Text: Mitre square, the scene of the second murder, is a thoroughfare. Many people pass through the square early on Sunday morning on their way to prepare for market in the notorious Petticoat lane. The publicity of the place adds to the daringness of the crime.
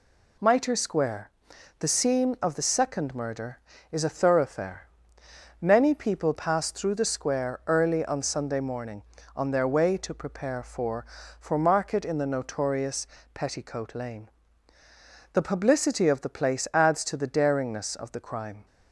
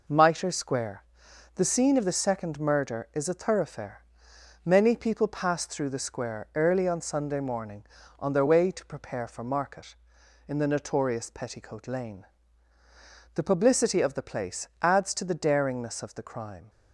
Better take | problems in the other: second | says "for" twice; at 11.3 s // pauses between "notorious" and "Petticoat"; slight; at 13.0 s; 0.26 s long

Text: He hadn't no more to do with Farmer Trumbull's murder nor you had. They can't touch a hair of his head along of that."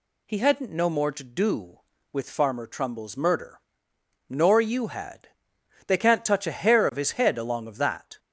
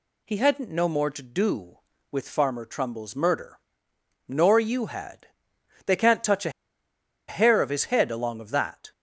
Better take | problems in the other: first | pauses between "murder" and "nor"; noticeable; at 3.5 s; 0.68 s long; noticeable in the first // pauses between "a" and "hair"; noticeable; at 6.4 s; 0.78 s long

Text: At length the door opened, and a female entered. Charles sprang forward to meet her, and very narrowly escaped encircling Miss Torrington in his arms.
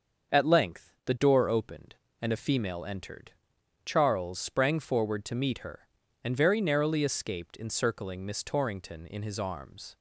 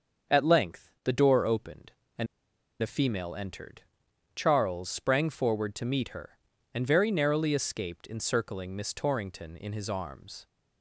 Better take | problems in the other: first | starts louder than the rest; until 1.4 s; 6.5 dB; also in the first // pauses between "and" and "a"; noticeable; at 2.2 s; 0.55 s long

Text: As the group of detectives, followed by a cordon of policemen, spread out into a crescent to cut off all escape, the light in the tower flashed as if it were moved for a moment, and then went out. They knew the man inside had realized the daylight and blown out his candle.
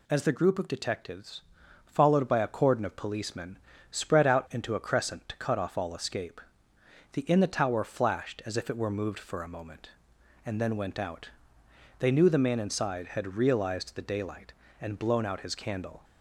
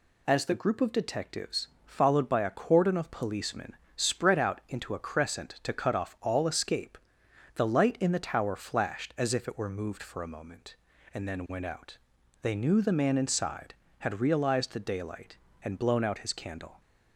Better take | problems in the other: second | skips "light"; at 7.2 s

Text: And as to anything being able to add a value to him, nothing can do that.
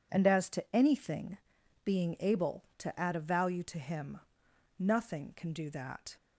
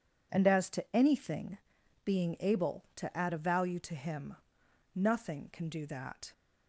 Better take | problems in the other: neither | pauses between "anything" and "being"; noticeable; the same in both

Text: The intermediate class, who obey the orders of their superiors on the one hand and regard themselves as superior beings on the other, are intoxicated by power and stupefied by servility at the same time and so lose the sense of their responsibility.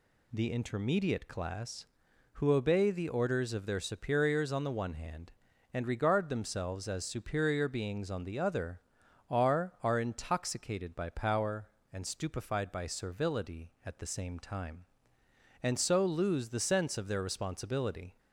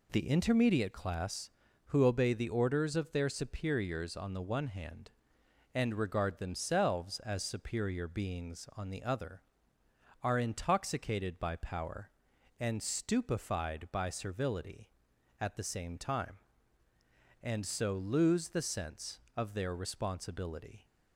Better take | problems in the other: second | says "are" twice; at 9.8 s

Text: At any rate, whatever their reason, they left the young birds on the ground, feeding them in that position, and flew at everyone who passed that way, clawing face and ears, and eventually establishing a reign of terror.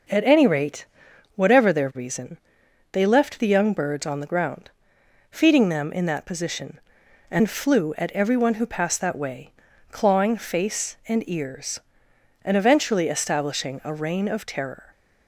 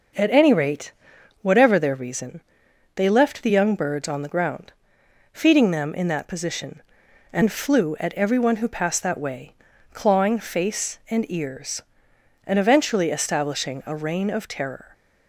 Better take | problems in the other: neither | starts louder than the rest; noticeable; the same in both

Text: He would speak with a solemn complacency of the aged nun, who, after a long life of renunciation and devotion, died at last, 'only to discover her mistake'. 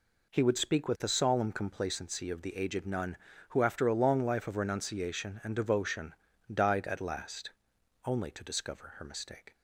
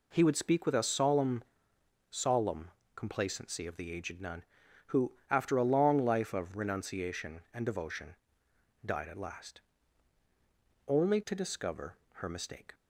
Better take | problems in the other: first | says "solemn" twice; at 2.1 s // pauses between "discover" and "her"; slight; at 11.9 s; 0.16 s long

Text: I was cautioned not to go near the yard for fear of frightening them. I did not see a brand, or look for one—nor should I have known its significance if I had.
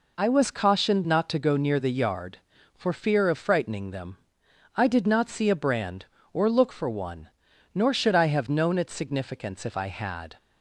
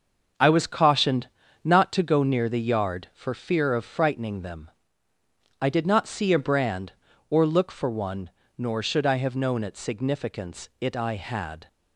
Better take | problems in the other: first | starts louder than the rest; noticeable; until 1.7 s; 6 dB // pauses between "cautioned" and "not"; slight; at 1.2 s; 0.34 s long // says "it" for "if"; at 10.7 s

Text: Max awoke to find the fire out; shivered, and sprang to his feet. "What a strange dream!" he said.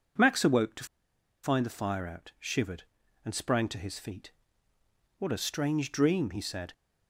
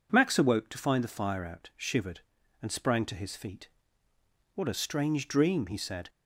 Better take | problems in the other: second | pauses between "to" and "find"; noticeable; at 0.8 s; 0.58 s long

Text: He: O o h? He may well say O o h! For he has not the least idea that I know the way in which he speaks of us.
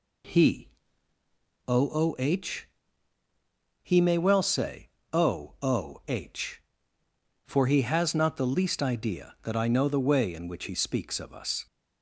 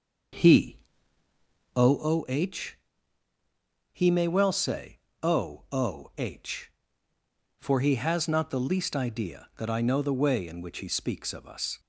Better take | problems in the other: first | starts louder than the rest; until 2.2 s; 6 dB // pauses between "say" and "O"; slight; at 4.9 s; 0.24 s long; slight in the first

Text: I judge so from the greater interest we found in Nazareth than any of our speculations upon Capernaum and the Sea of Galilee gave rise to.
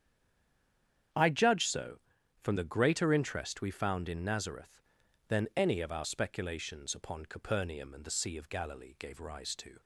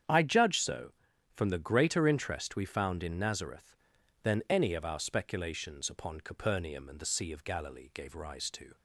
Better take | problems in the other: second | stays silent before the first word; until 1.1 s; 1.1 s long // starts louder than the rest; strong; until 2.5 s; 8.5 dB; strong in the second

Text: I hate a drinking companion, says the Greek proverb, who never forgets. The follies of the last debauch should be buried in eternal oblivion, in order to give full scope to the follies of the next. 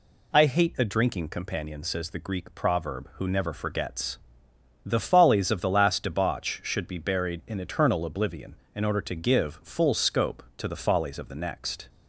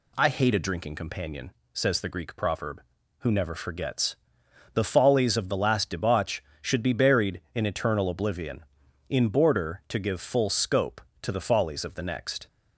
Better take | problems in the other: first | says "border" for "order"; at 9.2 s

